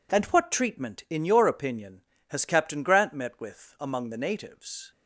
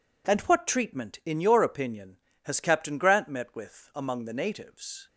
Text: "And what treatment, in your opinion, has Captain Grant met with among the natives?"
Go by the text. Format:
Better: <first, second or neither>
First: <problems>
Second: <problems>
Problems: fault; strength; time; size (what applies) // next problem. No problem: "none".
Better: neither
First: none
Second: none